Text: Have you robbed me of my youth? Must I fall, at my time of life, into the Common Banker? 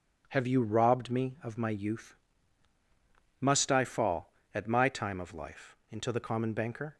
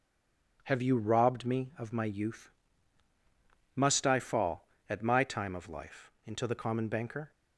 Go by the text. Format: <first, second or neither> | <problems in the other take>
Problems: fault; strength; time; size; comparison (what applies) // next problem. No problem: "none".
first | stays silent before the first word; slight; until 0.5 s; 0.5 s long